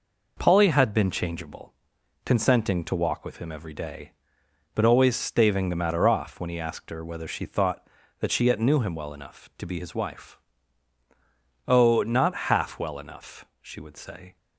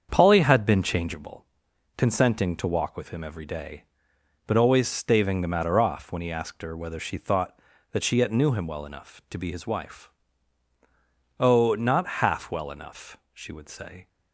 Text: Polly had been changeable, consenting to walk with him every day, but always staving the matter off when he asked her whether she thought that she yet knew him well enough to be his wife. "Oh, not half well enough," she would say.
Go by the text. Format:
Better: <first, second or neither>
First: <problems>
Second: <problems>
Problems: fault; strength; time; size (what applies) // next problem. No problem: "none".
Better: first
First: none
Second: starts louder than the rest; strong; until 1.2 s; 7 dB